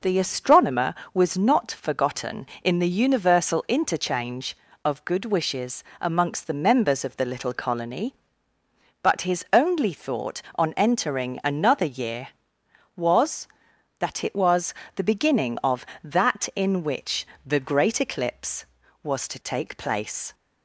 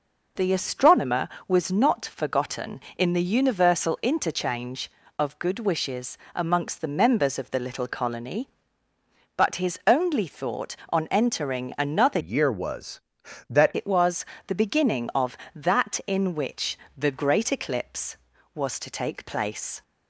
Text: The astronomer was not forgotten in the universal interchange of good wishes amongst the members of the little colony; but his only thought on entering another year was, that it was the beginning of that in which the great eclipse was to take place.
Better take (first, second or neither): first